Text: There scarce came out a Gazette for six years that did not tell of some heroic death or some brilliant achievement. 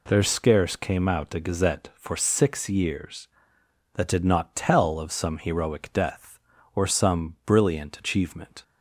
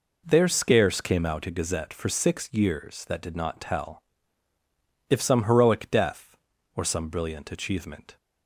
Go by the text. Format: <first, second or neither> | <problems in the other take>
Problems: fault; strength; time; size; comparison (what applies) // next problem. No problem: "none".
first | says "if" for "of"; at 5.1 s